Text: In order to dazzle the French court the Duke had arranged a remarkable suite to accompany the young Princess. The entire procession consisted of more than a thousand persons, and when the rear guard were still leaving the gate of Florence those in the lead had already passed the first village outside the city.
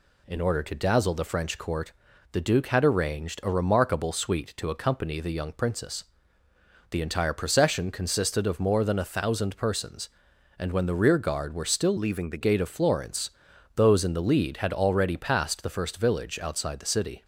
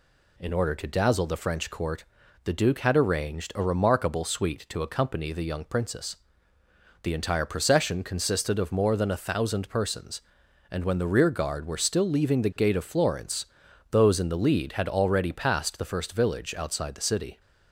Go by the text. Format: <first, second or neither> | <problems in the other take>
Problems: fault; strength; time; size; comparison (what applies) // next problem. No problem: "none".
second | pauses between "court" and "the"; at 1.9 s; 0.40 s long; also in the second // changes voice from "leaving" to "the"; from 11.9 to 12.4 s; 0.5 s long // pauses between "Florence" and "those"; noticeable; at 13.3 s; 0.46 s long; noticeable in the second